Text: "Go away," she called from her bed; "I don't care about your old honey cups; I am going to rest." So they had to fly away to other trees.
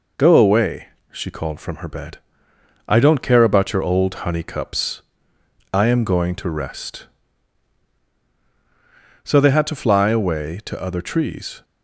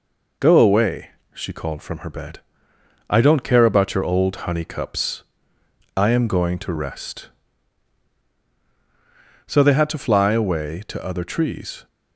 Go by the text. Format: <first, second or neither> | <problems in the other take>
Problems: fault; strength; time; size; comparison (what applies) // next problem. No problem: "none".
neither | none